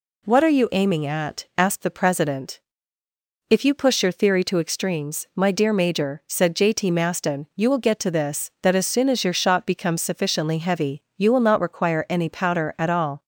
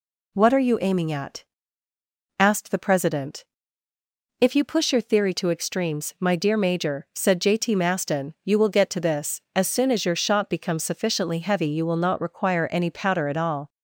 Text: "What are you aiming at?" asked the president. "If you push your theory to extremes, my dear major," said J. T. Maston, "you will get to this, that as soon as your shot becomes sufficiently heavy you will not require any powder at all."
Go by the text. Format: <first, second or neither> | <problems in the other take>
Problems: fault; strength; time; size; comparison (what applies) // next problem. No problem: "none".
first | skips "that"; at 9.4 s